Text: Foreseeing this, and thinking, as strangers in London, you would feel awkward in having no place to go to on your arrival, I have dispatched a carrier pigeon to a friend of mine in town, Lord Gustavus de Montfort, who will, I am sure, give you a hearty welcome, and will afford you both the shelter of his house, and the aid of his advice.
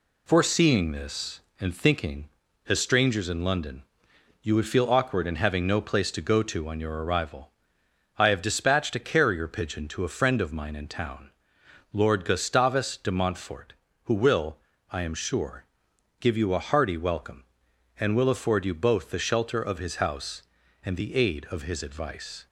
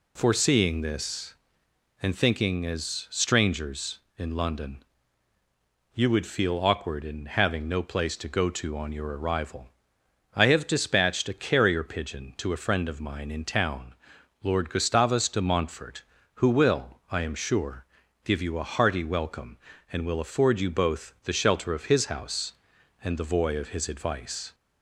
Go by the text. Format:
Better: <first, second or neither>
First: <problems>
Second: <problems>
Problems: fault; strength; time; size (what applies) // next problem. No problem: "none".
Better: first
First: none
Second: says "voy" for "aid"; at 23.3 s